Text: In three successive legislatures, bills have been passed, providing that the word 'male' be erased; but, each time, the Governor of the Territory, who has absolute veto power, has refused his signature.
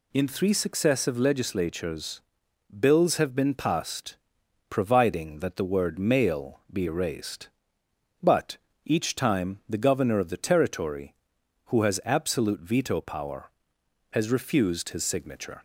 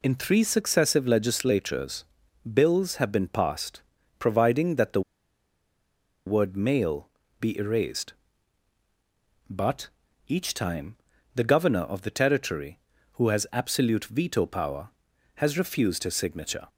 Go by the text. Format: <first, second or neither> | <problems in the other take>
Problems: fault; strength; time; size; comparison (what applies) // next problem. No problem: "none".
first | pauses between "the" and "word"; strong; at 5.0 s; 1.2 s long // pauses between "male" and "be"; slight; at 7.1 s; 0.30 s long